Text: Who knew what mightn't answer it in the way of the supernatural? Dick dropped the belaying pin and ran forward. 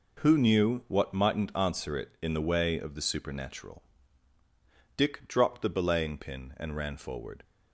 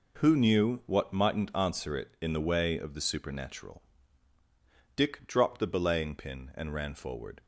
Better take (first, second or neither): neither